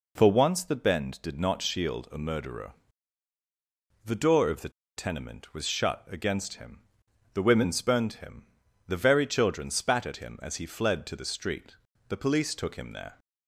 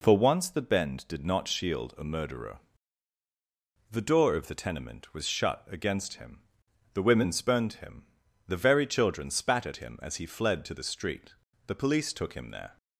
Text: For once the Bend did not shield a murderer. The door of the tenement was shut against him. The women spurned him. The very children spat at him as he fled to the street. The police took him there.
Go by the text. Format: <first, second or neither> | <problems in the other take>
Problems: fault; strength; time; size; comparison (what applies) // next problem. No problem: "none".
second | pauses between "the" and "tenement"; slight; at 4.7 s; 0.26 s long